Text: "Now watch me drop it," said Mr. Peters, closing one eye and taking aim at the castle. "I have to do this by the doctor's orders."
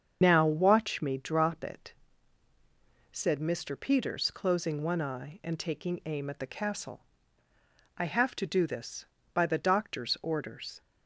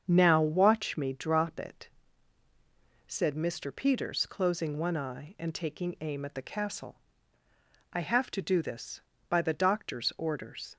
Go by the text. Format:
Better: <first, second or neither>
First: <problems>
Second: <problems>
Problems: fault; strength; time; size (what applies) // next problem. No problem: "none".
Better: second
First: loses the start of "Now"; at 0.2 s; 90 ms // starts louder than the rest; strong; until 1.2 s; 7 dB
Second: starts louder than the rest; strong; until 1.0 s; 7 dB